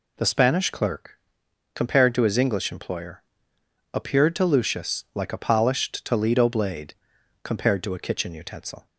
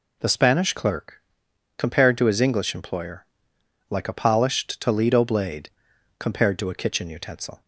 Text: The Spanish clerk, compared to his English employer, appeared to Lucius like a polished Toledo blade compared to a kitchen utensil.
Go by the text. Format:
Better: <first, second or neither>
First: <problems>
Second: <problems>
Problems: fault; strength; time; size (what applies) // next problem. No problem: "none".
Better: first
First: pauses between "blade" and "compared"; noticeable; at 6.9 s; 0.50 s long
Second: skips "appeared to Lucius"; at 3.5 s // pauses between "blade" and "compared"; noticeable; at 5.6 s; 0.50 s long